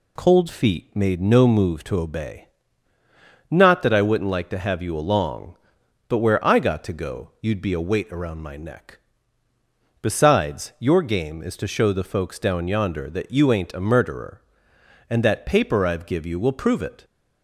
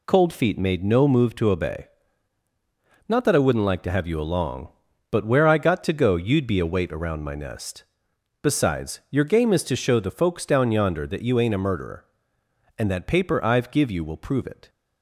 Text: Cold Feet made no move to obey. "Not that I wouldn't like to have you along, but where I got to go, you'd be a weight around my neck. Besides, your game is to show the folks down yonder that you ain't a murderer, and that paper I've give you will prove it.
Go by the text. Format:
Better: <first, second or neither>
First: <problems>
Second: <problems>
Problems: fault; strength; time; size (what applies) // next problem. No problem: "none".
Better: first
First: none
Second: says "nest" for "neck"; at 7.3 s